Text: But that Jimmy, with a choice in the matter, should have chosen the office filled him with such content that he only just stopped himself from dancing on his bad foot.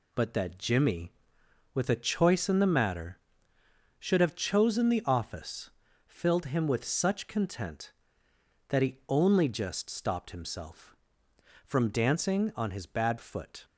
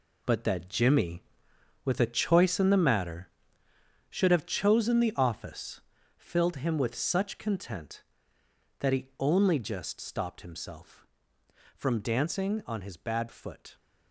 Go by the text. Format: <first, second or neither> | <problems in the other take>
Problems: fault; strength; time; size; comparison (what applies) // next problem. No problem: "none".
first | gets quieter; strong; throughout; 9.5 dB // pauses between "office" and "filled"; slight; at 5.8 s; 0.36 s long; slight in the first